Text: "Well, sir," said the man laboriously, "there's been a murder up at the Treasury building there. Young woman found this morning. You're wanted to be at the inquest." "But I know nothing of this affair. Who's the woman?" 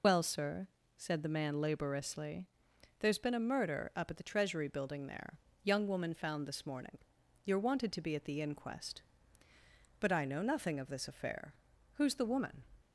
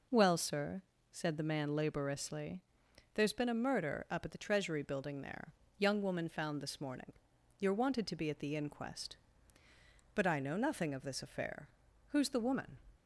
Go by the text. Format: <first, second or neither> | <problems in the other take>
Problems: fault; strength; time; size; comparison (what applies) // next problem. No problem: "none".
second | loses the start of "Well"; at 0.0 s; 95 ms